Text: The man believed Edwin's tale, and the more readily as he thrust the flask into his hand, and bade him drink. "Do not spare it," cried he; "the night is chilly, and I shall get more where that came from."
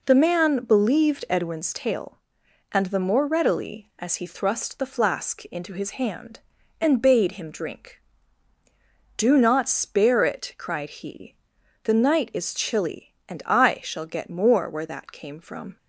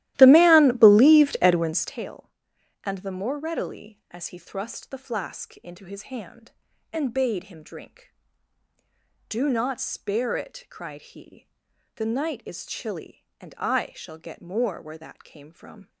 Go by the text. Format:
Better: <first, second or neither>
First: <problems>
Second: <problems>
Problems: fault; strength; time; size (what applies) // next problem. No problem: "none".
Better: first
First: none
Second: starts louder than the rest; strong; until 2.0 s; 15 dB